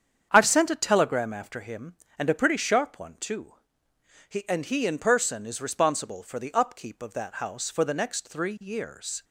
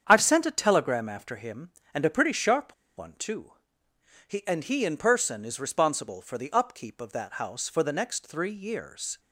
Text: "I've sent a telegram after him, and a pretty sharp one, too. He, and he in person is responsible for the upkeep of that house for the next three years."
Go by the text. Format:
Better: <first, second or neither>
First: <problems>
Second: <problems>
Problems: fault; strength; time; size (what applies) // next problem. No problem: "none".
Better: first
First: starts louder than the rest; strong; until 1.3 s; 8 dB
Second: starts louder than the rest; strong; until 1.0 s; 8 dB // pauses between "sharp" and "one"; slight; at 2.7 s; 0.23 s long